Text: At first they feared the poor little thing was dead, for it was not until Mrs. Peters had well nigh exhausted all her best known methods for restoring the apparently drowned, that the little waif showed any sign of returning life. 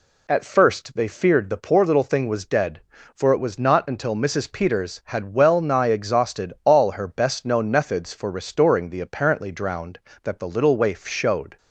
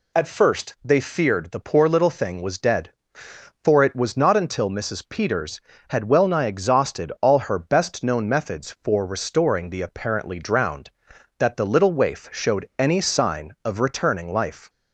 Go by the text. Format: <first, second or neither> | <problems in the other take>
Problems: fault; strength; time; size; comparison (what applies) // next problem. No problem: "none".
second | stops before "any sign of returning life"; at 11.5 s